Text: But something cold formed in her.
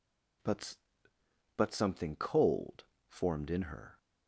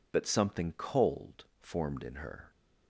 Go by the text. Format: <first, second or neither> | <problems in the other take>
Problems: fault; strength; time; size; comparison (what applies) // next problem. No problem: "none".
second | says "But" twice; at 1.5 s // pauses between "cold" and "formed"; slight; at 2.8 s; 0.20 s long; slight in the second